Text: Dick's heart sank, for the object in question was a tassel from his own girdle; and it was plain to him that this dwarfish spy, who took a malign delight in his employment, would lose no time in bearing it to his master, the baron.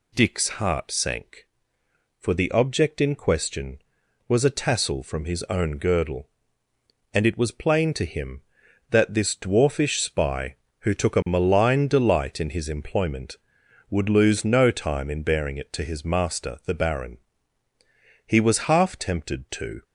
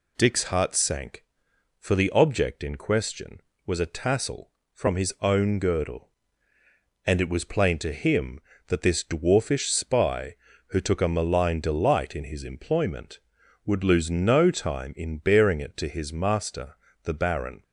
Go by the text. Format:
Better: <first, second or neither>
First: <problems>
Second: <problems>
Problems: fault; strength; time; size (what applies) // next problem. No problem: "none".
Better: second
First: goes on to say "He was half tempted to"; from 18.2 s on; 1.5 s long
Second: none